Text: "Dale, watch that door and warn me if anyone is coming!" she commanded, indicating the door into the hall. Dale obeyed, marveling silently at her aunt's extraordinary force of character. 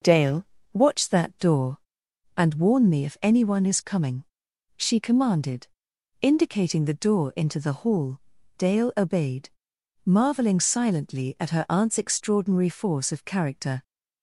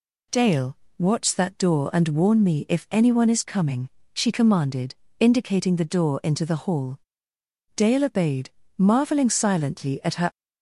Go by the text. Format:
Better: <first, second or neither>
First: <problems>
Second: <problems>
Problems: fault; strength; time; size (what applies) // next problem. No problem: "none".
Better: first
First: none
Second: stops before "aunt's extraordinary force of character"; at 10.3 s